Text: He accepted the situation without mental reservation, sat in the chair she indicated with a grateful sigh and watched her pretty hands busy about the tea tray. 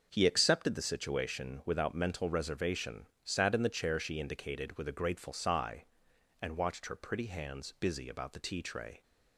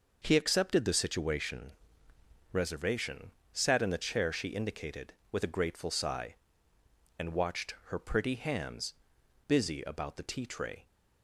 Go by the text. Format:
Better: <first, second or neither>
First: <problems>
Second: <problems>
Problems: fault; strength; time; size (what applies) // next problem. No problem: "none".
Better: first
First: starts louder than the rest; until 1.1 s; 6 dB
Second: starts louder than the rest; noticeable; until 1.2 s; 6 dB // skips "without mental"; at 2.1 s // pauses between "hands" and "busy"; noticeable; at 8.9 s; 0.54 s long